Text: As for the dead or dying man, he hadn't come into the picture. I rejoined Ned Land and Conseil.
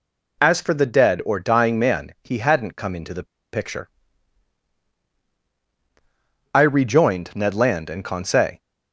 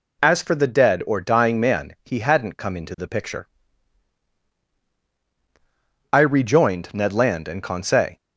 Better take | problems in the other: second | pauses between "the" and "picture"; slight; at 3.2 s; 0.28 s long

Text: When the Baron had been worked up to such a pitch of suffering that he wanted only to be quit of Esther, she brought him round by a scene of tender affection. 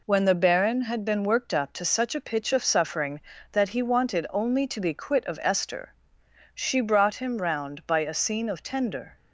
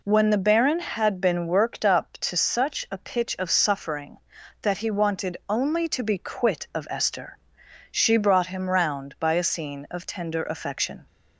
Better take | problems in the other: second | stops before "affection"; at 9.1 s

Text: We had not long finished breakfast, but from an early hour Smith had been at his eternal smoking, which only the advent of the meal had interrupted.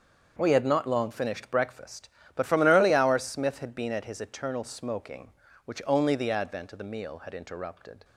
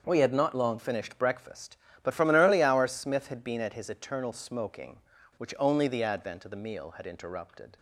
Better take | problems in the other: neither | starts louder than the rest; the same in both

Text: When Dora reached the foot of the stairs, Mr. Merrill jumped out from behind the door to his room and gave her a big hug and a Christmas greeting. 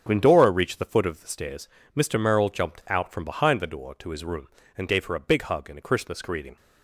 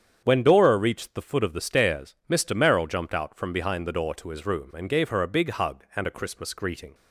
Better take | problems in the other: neither | starts louder than the rest; the same in both

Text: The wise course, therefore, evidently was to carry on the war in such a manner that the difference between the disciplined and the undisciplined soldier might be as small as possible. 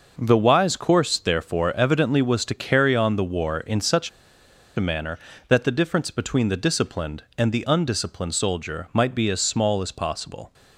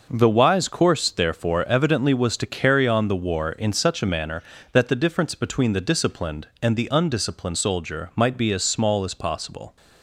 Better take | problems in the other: second | pauses between "such" and "a"; noticeable; at 4.0 s; 0.67 s long

